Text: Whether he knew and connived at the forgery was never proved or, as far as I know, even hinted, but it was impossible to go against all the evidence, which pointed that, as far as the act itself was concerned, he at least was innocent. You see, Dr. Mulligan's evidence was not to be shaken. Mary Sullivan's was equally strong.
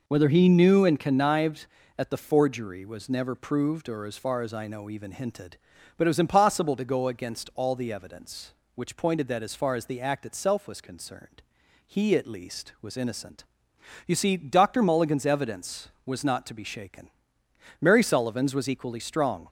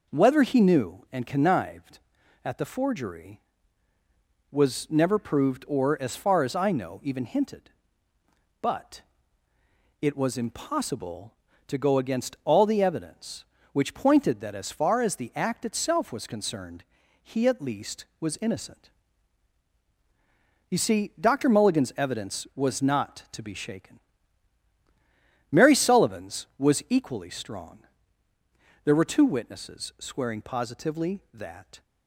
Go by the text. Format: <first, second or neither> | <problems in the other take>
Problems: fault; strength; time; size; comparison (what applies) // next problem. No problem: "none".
first | pauses between "but" and "it"; noticeable; at 9.0 s; 0.98 s long // goes on to say "There were two witnesses swearing positively that"; strong; from 28.8 s on; 2.9 s long